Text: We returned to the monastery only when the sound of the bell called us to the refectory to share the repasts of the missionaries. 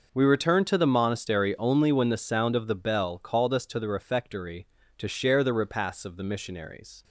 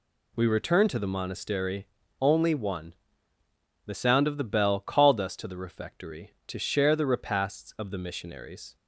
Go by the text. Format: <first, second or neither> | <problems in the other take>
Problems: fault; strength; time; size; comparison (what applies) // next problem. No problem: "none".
first | pauses between "monastery" and "only"; slight; at 1.8 s; 0.34 s long // says "one" for "when"; at 2.5 s